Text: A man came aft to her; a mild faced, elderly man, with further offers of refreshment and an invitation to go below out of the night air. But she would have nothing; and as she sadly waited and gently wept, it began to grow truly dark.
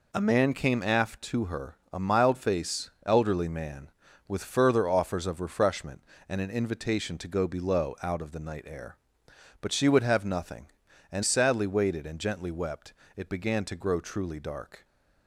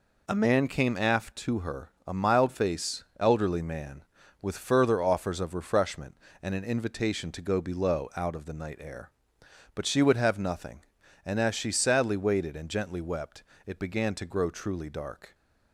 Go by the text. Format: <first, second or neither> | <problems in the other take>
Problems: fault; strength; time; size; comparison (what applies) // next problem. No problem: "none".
second | skips "as she"; at 11.2 s